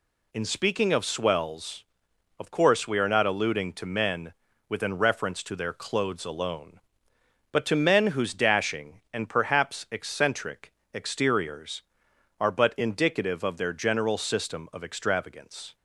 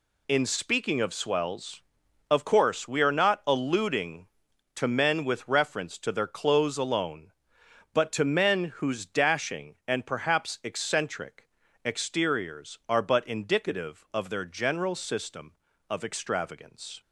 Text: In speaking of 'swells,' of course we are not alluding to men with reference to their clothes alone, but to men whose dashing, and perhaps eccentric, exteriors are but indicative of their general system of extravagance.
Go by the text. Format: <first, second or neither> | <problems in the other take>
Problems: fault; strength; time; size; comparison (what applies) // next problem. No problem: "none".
second | says "within" for "with"; at 4.6 s